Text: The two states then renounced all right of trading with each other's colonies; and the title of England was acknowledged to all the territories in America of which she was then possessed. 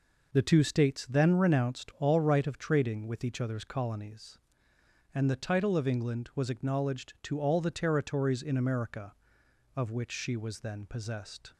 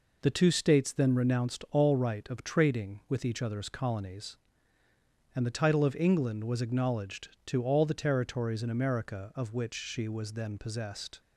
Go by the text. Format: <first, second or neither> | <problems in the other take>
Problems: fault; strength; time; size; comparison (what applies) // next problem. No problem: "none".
neither | none